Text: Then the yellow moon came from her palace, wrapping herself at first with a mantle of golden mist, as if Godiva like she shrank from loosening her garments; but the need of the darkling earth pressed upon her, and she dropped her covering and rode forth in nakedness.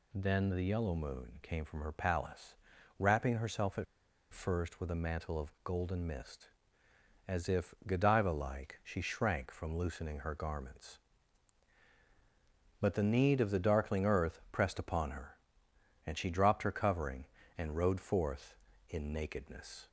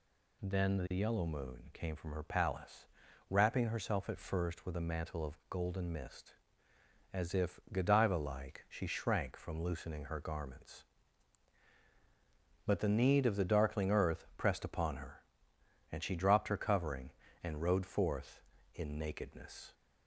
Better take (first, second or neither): second